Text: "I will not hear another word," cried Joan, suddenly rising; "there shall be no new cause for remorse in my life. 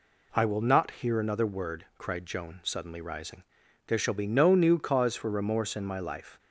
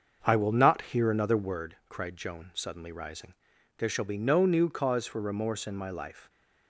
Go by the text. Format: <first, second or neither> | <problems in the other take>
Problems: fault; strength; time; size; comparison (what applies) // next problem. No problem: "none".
first | starts louder than the rest; until 1.6 s; 6.5 dB